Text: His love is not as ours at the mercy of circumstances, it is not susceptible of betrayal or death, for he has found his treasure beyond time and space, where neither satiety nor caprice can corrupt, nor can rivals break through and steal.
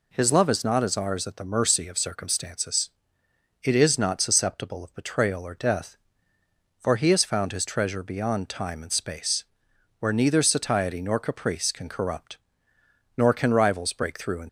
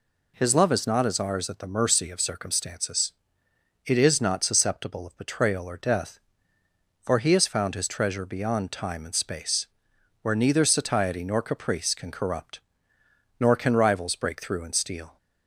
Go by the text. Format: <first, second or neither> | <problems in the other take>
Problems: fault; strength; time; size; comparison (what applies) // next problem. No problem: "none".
second | stops before "steal"; at 14.4 s